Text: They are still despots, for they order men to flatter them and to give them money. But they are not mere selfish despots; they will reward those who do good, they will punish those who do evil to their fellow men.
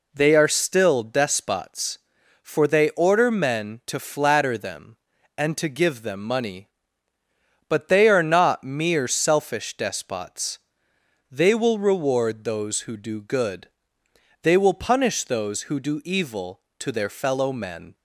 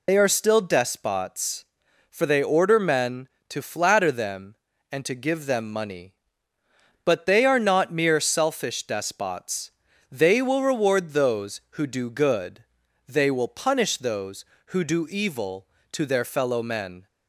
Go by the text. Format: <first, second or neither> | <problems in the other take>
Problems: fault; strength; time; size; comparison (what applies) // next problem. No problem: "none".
first | loses the start of "They"; at 0.0 s; 80 ms